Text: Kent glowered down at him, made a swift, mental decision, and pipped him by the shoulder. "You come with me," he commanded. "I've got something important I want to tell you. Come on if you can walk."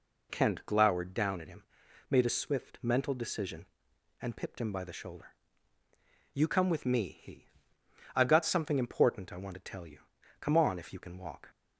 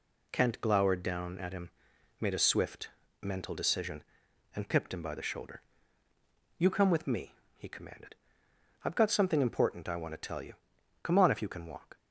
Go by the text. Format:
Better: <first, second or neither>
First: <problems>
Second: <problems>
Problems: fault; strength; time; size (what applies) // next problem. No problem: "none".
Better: second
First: skips "commanded"; at 7.8 s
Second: none